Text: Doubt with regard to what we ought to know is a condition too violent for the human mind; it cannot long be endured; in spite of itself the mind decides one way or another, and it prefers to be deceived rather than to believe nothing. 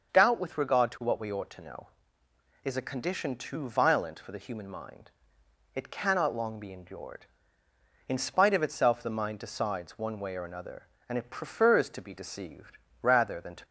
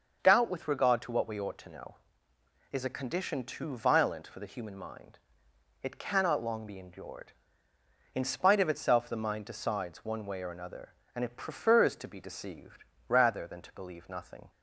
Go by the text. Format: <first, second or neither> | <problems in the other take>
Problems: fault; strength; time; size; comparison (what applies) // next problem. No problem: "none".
second | starts louder than the rest; until 1.1 s; 6.5 dB; also in the second // pauses between "deceived" and "rather"; slight; at 12.7 s; 0.26 s long; slight in the second // stops before "believe nothing"; at 13.6 s